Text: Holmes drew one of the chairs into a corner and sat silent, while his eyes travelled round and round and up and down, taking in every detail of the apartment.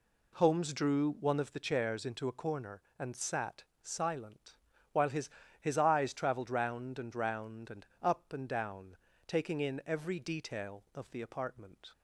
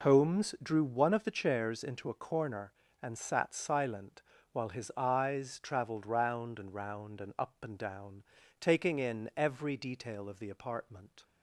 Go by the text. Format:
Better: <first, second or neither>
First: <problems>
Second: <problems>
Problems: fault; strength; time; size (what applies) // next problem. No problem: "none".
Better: second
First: pauses between "sat" and "silent"; slight; at 3.6 s; 0.18 s long // says "his" twice; at 5.6 s // pauses between "and" and "up"; slight; at 7.8 s; 0.16 s long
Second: none